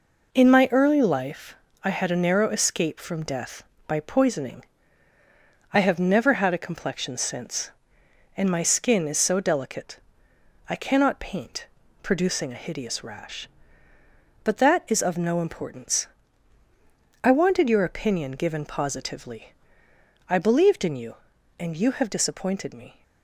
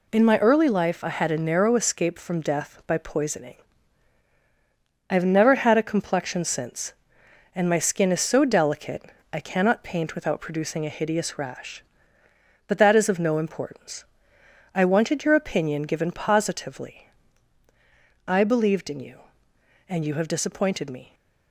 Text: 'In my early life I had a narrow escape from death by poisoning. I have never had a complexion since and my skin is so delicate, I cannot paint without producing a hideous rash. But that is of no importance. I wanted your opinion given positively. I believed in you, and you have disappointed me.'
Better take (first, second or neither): second